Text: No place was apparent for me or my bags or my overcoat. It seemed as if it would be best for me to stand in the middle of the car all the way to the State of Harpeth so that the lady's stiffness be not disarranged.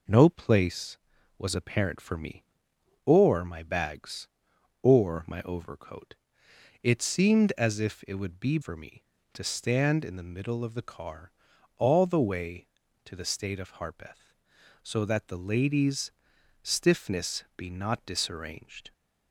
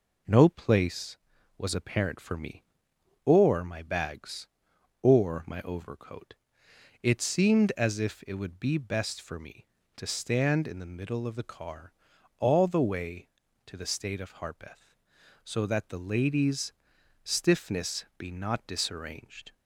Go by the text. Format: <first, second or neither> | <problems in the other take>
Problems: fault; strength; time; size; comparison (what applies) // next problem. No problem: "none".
second | skips "best"; at 8.5 s // pauses between "car" and "all"; noticeable; at 11.3 s; 0.48 s long; noticeable in the second // pauses between "lady's" and "stiffness"; noticeable; at 16.1 s; 0.54 s long; noticeable in the second